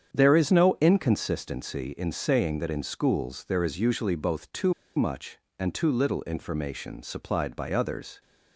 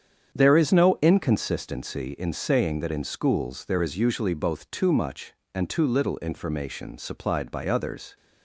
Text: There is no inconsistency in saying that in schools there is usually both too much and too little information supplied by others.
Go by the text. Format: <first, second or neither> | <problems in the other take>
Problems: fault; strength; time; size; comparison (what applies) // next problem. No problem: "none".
second | starts louder than the rest; strong; until 1.1 s; 8 dB; strong in the second // pauses between "too" and "much"; slight; at 4.7 s; 0.23 s long